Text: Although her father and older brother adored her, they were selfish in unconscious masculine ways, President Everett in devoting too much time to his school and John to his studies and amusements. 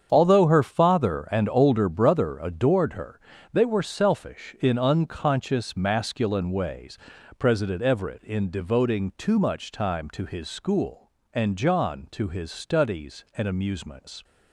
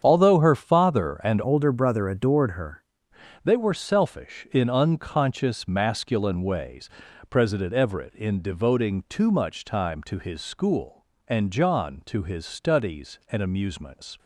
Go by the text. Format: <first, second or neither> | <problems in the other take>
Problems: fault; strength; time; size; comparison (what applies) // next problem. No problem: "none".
first | starts louder than the rest; strong; until 1.0 s; 8 dB; strong in the first // changes voice from "older" to "her"; from 1.4 to 2.8 s; 1.4 s long